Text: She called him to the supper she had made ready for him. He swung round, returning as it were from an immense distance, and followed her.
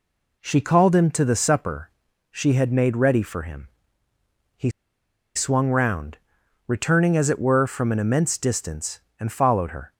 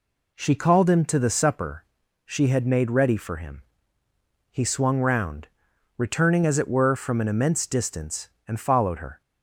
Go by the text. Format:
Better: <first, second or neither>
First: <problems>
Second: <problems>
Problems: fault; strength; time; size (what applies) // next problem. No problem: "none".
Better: second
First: pauses between "supper" and "she"; at 1.8 s; 0.42 s long // pauses between "He" and "swung"; noticeable; at 4.6 s; 0.66 s long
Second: pauses between "supper" and "she"; at 1.8 s; 0.42 s long